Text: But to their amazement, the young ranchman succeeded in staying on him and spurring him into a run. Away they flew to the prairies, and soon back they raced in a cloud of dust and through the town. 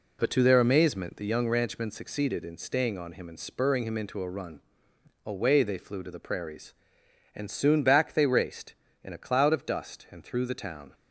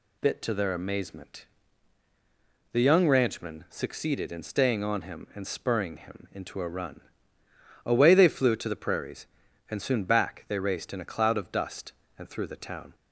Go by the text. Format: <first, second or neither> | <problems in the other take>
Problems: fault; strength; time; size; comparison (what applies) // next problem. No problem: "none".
first | says "Bit" for "But"; at 0.2 s